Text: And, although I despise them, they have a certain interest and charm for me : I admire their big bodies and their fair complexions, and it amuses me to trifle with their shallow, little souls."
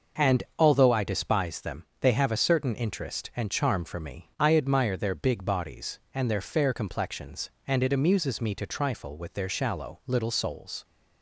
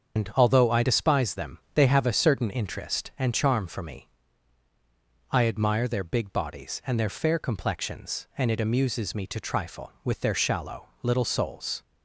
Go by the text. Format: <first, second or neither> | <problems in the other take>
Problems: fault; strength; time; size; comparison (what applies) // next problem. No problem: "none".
first | loses the start of "And"; at 0.1 s; 125 ms // starts louder than the rest; strong; until 1.2 s; 7 dB